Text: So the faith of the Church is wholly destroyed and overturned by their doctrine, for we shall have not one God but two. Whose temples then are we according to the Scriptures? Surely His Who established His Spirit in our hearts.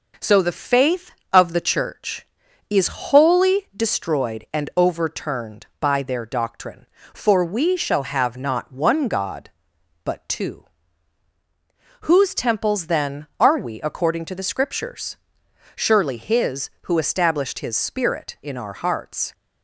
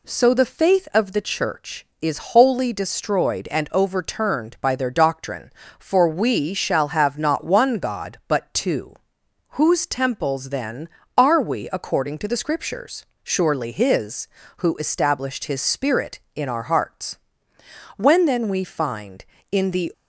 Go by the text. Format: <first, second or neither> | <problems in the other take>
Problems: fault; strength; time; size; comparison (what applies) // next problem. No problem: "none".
first | goes on to say "When then we find in the"; strong; from 17.9 s on; 1.9 s long